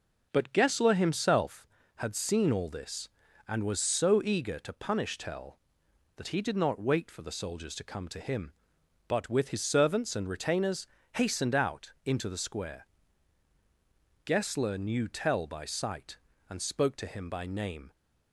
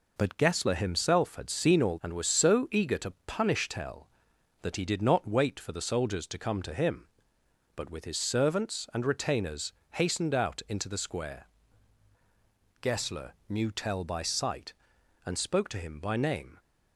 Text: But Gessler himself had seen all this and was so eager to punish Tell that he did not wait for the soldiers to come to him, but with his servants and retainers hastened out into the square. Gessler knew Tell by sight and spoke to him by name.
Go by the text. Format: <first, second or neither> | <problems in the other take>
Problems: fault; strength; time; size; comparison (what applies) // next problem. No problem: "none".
first | skips "this"; at 1.9 s // pauses between "retainers" and "hastened"; slight; at 9.7 s; 0.20 s long; slight in the first // pauses between "Gessler" and "knew"; slight; at 13.3 s; 0.16 s long